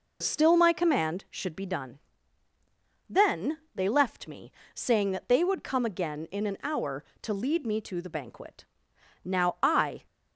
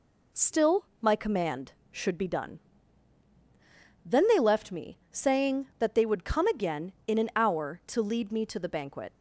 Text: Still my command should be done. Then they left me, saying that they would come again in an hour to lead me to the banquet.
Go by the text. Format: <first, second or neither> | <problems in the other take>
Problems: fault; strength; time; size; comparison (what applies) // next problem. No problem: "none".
second | pauses between "Then" and "they"; slight; at 3.5 s; 0.16 s long // goes on to say "Now I"; noticeable; from 9.2 s on; 0.80 s long